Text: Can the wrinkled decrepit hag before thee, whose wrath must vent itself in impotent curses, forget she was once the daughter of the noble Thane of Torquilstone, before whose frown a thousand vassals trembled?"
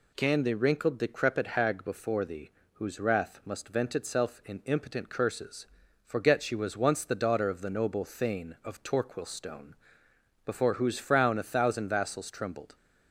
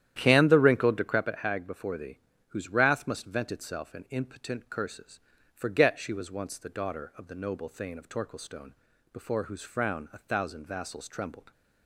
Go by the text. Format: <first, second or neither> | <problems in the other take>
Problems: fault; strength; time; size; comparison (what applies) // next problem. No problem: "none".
first | starts louder than the rest; strong; until 1.3 s; 11 dB